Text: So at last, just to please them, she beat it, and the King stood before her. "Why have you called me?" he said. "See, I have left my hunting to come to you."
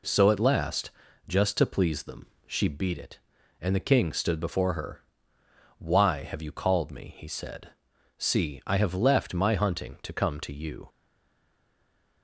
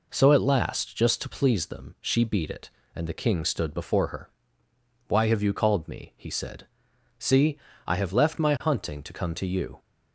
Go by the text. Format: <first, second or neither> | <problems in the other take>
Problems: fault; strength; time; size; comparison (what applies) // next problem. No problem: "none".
second | stays silent after the last word; noticeable; from 10.8 s on; 1.4 s long